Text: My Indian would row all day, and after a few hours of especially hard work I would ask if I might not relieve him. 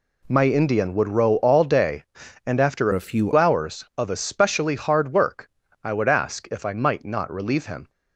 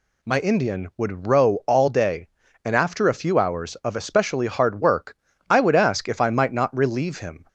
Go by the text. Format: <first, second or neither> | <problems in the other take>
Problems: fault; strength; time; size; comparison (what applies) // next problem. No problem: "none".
second | changes voice from "a" to "few"; from 2.9 to 3.3 s; 0.4 s long // pauses between "work" and "I"; slight; at 5.4 s; 0.34 s long; slight in the second